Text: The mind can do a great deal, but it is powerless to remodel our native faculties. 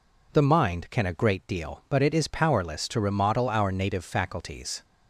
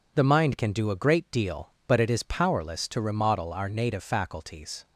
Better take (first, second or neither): second